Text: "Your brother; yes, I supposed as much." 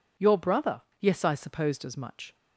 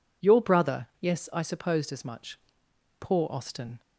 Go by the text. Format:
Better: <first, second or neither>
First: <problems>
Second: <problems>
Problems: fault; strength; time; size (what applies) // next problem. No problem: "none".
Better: first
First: none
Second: goes on to say "Poor Austin"; noticeable; from 3.0 s on; 0.80 s long